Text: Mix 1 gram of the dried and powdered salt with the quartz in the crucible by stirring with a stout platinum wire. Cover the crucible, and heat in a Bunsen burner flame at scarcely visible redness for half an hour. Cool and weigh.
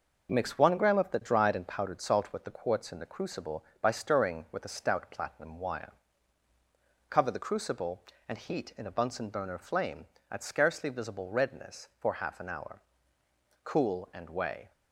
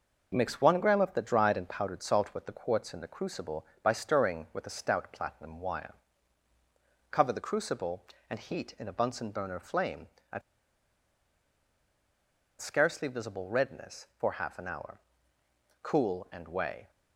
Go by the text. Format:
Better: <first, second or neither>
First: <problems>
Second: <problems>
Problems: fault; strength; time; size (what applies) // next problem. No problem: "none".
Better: first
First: none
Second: pauses between "at" and "scarcely"; strong; at 10.4 s; 2.1 s long